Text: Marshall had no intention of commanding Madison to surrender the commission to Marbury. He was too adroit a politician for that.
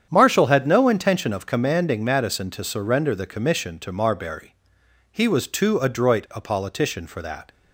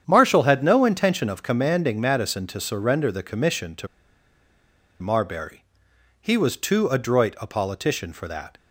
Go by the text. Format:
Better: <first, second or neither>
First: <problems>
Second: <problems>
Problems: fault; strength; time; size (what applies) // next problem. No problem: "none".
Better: first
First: starts louder than the rest; strong; until 1.1 s; 8.5 dB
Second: starts louder than the rest; strong; until 1.0 s; 8.5 dB // pauses between "to" and "Marbury"; at 3.8 s; 1.1 s long